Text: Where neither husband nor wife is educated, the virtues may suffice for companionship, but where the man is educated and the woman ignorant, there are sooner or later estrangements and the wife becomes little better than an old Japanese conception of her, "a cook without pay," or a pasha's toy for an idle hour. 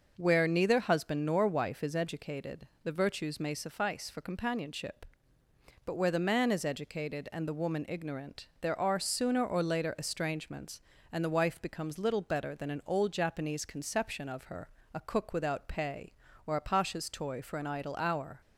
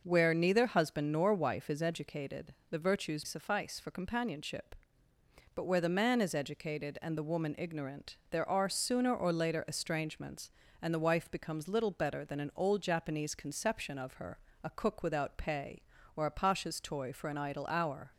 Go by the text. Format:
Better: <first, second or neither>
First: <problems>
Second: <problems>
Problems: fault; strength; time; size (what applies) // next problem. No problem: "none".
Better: first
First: none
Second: skips "may"; at 3.2 s